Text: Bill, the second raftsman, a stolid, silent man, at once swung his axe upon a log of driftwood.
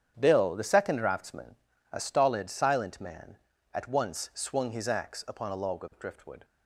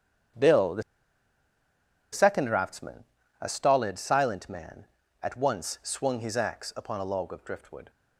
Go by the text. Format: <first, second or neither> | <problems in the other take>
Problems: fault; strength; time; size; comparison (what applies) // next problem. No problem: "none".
first | starts louder than the rest; strong; until 2.6 s; 8.5 dB; strong in the first // pauses between "the" and "second"; strong; at 0.8 s; 1.2 s long